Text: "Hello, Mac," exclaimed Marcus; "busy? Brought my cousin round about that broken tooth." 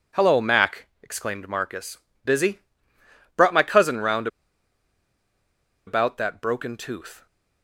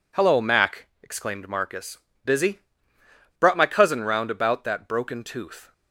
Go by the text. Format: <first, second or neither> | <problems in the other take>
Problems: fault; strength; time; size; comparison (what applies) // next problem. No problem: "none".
second | pauses between "round" and "about"; strong; at 4.2 s; 1.5 s long